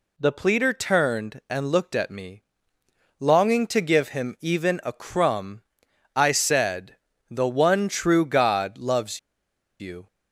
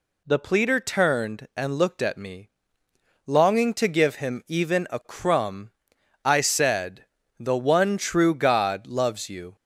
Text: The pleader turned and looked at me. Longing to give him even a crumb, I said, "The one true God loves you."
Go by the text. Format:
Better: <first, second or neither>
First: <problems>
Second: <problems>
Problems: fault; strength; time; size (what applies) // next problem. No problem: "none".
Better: second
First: pauses between "loves" and "you"; noticeable; at 9.1 s; 0.61 s long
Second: none